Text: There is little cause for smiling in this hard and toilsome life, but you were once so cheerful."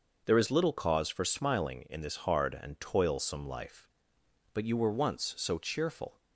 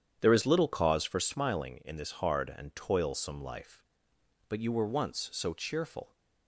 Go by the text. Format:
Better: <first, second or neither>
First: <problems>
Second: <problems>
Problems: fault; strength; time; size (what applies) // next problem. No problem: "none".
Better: first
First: none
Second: starts louder than the rest; strong; until 1.3 s; 9 dB